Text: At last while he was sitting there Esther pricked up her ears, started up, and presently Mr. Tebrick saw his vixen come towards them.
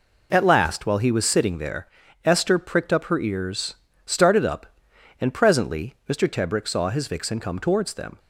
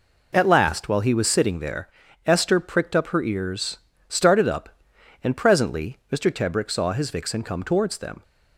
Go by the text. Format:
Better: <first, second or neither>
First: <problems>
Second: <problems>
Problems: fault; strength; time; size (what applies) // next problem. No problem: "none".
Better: neither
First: pauses between "there" and "Esther"; slight; at 1.8 s; 0.34 s long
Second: pauses between "there" and "Esther"; slight; at 1.9 s; 0.34 s long